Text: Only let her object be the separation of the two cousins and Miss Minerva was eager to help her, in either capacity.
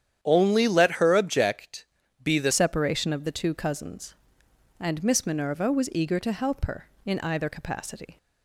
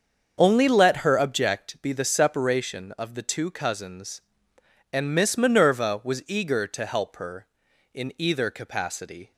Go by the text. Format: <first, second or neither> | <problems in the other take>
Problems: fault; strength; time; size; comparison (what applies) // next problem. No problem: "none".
second | starts louder than the rest; strong; until 1.2 s; 9.5 dB; also in the second // pauses between "object" and "be"; slight; at 1.8 s; 0.36 s long // changes voice at "separation"; from 2.5 s on; 5.6 s long